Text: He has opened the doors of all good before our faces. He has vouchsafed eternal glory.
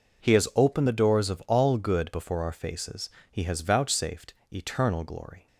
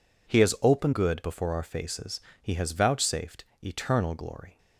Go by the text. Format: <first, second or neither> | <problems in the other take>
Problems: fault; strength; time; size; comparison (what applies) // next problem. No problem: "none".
first | skips "the doors of all"; at 0.9 s // pauses between "vouchsafed" and "eternal"; slight; at 3.4 s; 0.18 s long; slight in the first